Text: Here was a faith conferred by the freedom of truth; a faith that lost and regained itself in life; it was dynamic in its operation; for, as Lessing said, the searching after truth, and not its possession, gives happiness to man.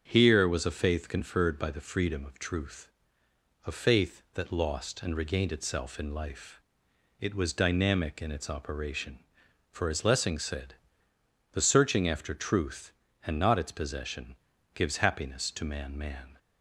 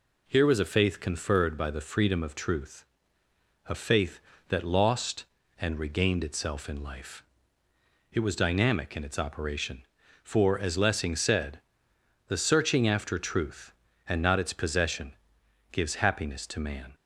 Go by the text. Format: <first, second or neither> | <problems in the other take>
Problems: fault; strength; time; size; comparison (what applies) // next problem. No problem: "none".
second | starts louder than the rest; until 1.0 s; 7 dB // says "man" twice; at 15.9 s